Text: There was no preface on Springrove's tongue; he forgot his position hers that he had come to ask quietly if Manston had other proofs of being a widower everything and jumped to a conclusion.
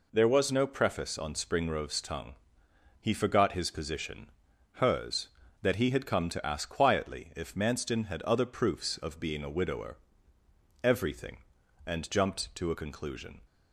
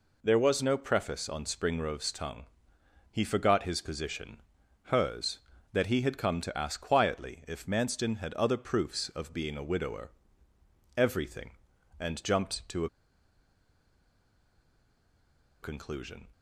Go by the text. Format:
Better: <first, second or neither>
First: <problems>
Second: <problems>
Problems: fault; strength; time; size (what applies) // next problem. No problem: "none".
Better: first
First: pauses between "position" and "hers"; noticeable; at 4.3 s; 0.46 s long // pauses between "widower" and "everything"; noticeable; at 9.9 s; 0.84 s long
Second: pauses between "position" and "hers"; noticeable; at 4.4 s; 0.46 s long // pauses between "widower" and "everything"; noticeable; at 10.1 s; 0.84 s long // pauses between "a" and "conclusion"; strong; at 12.8 s; 2.7 s long